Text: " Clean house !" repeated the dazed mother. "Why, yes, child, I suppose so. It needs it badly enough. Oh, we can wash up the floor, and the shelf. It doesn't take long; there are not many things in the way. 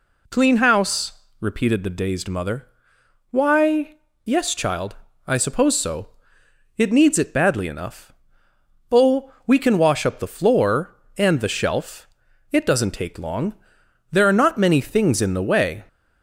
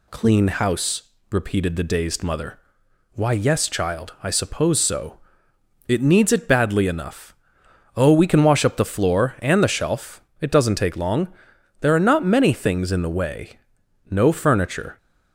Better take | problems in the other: first | goes on to say "No furniture"; noticeable; from 14.0 s on; 0.88 s long

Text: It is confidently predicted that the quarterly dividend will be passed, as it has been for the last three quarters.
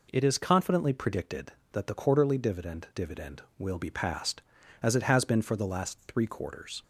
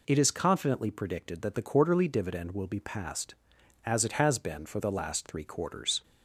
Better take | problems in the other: second | says "dividend" twice; at 2.9 s

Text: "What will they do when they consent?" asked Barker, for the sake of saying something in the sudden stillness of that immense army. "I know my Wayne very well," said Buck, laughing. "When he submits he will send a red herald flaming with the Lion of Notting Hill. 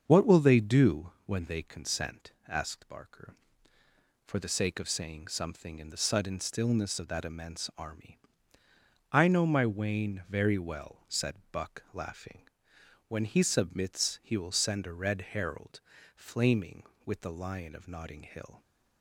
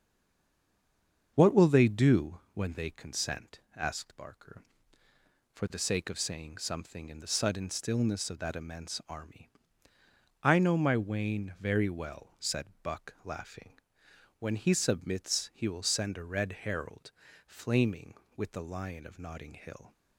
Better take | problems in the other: first | stays silent before the first word; noticeable; until 1.3 s; 1.3 s long // starts louder than the rest; until 2.3 s; 7 dB; also in the first // pauses between "herald" and "flaming"; slight; at 17.1 s; 0.34 s long; slight in the first

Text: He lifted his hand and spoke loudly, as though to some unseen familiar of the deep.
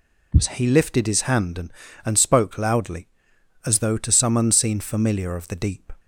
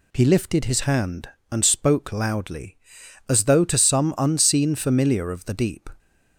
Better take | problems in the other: second | says "and" twice; at 2.0 s

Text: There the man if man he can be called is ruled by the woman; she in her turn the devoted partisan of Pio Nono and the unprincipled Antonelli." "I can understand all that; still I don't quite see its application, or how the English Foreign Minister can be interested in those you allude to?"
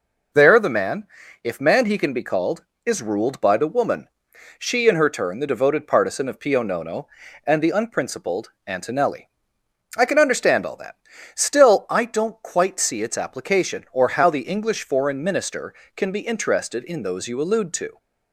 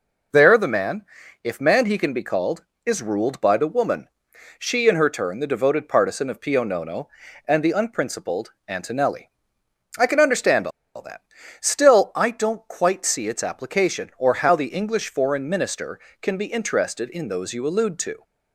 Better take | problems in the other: first | pauses between "man" and "if"; at 1.0 s; 0.38 s long; also in the first // pauses between "unprincipled" and "Antonelli"; slight; at 8.5 s; 0.16 s long; slight in the first // pauses between "understand" and "all"; slight; at 10.6 s; 0.26 s long

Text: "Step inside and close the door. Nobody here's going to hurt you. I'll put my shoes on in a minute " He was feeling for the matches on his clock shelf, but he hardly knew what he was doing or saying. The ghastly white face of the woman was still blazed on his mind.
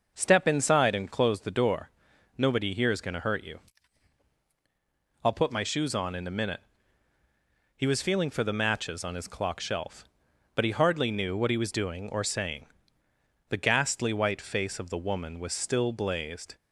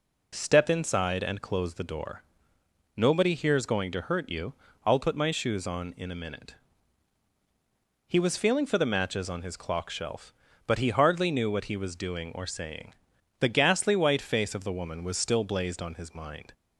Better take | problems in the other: second | starts louder than the rest; until 1.1 s; 6.5 dB // stops before "on his mind"; at 16.5 s

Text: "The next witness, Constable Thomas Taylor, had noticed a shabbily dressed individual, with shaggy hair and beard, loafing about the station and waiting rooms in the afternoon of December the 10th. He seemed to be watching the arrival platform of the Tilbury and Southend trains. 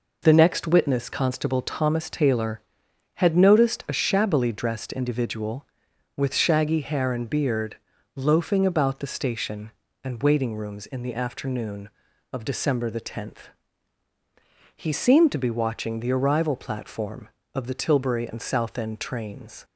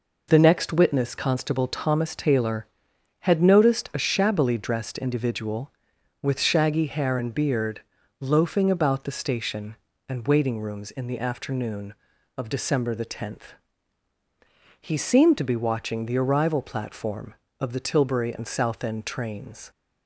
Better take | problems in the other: neither | none

